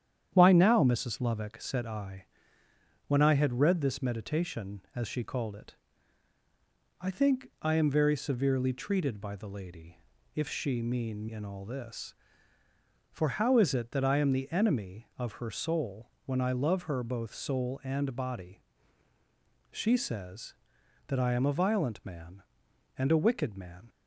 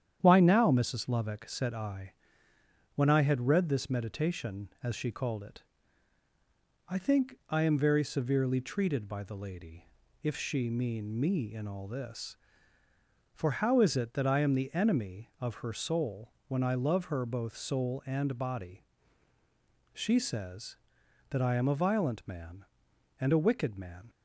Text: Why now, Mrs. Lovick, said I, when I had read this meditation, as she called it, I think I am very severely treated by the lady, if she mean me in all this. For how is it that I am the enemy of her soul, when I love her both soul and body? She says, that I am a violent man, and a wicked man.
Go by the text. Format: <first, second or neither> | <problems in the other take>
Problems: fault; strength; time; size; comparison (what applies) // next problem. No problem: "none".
second | starts louder than the rest; strong; until 1.3 s; 9.5 dB; strong in the second // skips "me"; at 11.2 s